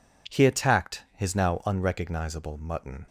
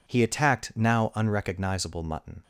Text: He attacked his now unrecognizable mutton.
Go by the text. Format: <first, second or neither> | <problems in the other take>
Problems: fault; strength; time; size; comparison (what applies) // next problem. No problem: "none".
first | skips "his"; at 0.7 s